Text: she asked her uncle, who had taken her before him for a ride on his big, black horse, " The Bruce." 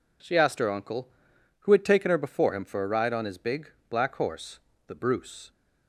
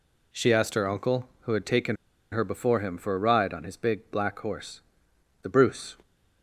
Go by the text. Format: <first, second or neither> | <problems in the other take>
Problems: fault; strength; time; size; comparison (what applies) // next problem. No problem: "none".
first | pauses between "taken" and "her"; slight; at 1.9 s; 0.35 s long